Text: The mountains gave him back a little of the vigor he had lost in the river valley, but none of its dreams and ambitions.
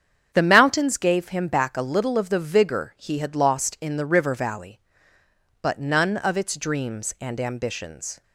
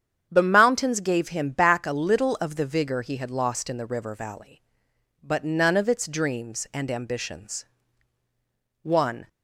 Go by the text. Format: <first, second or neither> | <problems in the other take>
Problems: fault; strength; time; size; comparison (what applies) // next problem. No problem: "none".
first | starts louder than the rest; strong; until 1.3 s; 8 dB; strong in the first // goes on to say "One"; slight; from 8.8 s on; 0.46 s long